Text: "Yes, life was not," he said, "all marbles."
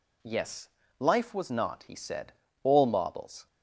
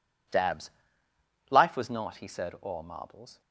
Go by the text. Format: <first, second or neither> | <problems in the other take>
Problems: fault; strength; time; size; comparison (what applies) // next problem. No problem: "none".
first | says "Dabs" for "Yes"; at 0.2 s